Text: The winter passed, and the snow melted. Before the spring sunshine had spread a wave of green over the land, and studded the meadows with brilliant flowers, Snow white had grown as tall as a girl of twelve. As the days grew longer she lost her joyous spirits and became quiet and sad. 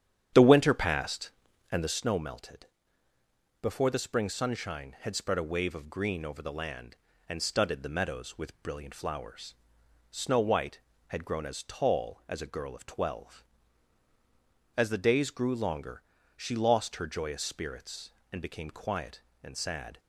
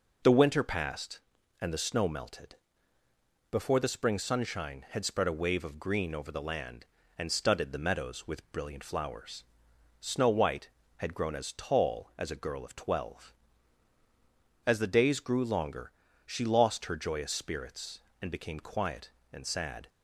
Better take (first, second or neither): second